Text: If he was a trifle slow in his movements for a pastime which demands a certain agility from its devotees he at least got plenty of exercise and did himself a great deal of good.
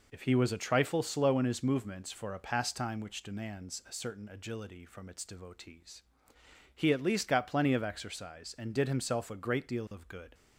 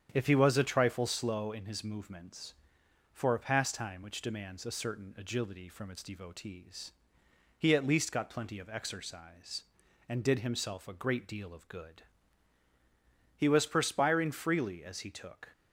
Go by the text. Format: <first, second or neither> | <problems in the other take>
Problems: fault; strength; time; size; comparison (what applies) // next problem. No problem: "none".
first | starts louder than the rest; strong; until 1.1 s; 8.5 dB // pauses between "devotees" and "he"; noticeable; at 6.9 s; 0.66 s long; noticeable in the first // goes on to say "He was perspiring freely as he took"; strong; from 13.3 s on; 2.1 s long